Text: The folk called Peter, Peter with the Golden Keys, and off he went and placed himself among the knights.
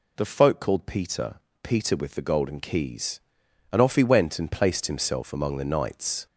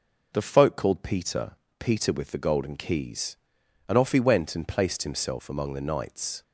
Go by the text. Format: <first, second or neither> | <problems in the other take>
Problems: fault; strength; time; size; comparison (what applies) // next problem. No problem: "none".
second | gets louder; slight; throughout; 3.5 dB